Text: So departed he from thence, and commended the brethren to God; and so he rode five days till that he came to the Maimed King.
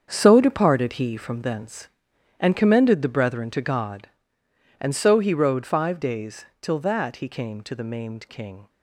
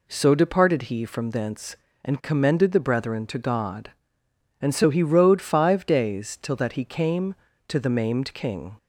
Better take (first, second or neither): second